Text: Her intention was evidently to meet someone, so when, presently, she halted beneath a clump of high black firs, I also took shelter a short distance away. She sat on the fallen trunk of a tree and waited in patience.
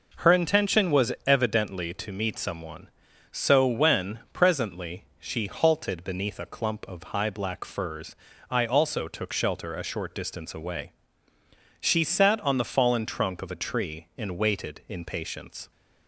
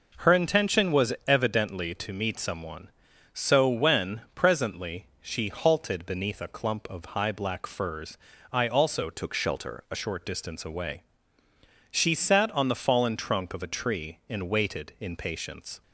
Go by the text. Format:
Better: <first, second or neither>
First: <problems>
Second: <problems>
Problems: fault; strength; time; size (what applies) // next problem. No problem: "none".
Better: first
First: none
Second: changes voice from "took" to "a"; from 9.1 to 9.9 s; 0.8 s long